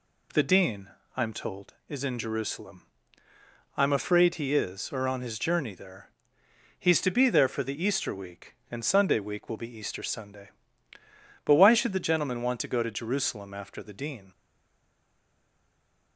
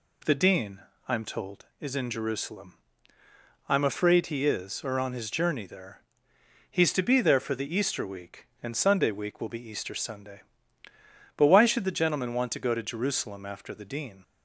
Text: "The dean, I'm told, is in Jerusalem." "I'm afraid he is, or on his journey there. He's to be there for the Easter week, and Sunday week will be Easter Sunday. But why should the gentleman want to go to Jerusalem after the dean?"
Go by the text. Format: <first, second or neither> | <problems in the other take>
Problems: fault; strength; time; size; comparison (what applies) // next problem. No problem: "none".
second | stays silent after the last word; noticeable; from 14.3 s on; 1.8 s long